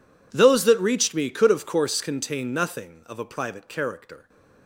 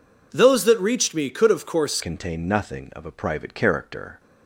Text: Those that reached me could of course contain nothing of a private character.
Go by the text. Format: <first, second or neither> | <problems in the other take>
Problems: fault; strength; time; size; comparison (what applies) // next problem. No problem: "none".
first | changes voice at "contain"; from 2.0 s on; 2.1 s long